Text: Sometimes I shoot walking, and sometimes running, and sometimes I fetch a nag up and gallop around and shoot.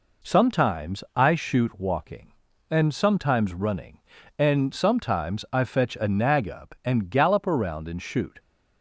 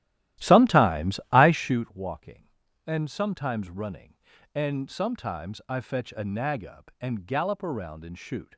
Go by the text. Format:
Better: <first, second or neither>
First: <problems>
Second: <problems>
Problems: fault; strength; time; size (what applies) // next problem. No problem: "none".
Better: first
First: none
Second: starts louder than the rest; strong; until 1.9 s; 14 dB